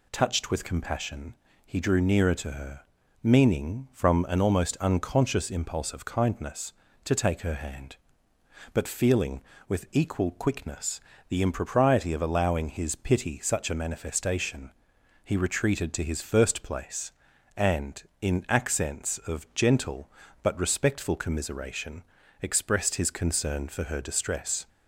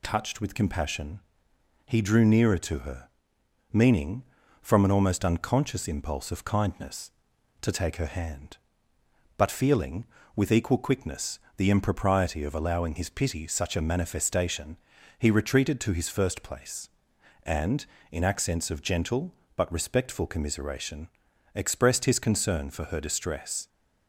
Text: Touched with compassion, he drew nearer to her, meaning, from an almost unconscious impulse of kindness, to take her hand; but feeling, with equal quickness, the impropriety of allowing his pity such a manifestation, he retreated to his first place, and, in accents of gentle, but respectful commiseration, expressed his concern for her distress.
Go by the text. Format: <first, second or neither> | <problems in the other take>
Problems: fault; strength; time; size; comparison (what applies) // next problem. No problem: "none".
neither | none